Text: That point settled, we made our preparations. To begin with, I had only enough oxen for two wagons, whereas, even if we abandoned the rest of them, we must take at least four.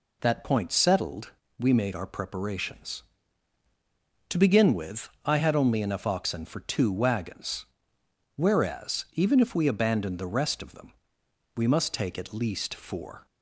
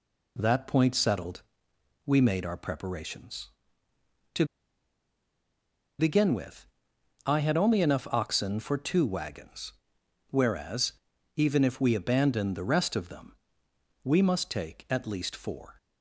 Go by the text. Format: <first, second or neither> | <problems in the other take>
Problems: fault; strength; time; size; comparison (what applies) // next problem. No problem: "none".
first | pauses between "To" and "begin"; strong; at 4.4 s; 1.5 s long